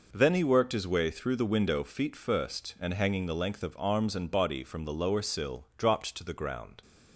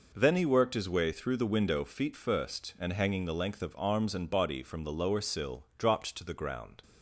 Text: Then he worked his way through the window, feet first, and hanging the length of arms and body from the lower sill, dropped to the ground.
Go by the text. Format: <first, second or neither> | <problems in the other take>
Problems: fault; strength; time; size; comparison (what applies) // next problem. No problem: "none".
neither | none